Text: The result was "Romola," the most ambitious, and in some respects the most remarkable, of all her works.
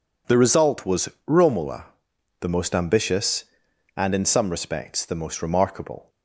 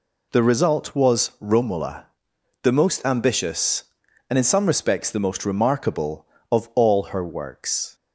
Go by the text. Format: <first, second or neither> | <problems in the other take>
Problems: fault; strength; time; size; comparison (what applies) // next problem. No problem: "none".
second | pauses between "was" and "Romola"; slight; at 1.0 s; 0.20 s long // stops before "of all her works"; at 6.0 s